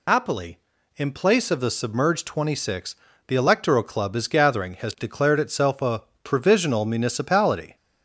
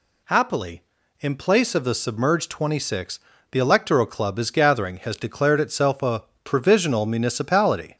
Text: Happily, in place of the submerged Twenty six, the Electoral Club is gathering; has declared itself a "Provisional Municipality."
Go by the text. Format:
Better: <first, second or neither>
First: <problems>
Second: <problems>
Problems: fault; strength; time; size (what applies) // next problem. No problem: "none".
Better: second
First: loses the start of "Happily"; at 0.0 s; 65 ms // pauses between "a" and "Provisional"; slight; at 6.0 s; 0.22 s long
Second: pauses between "a" and "Provisional"; slight; at 6.2 s; 0.22 s long